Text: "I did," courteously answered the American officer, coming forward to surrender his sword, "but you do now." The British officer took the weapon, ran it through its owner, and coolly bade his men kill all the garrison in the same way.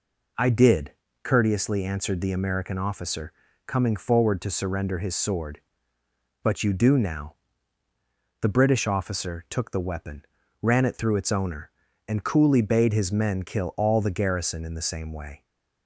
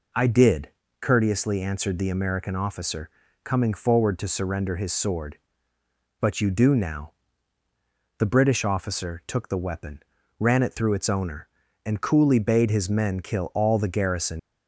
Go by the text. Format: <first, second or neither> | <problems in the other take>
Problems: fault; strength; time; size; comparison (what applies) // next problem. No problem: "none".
first | stops before "in the same way"; at 14.3 s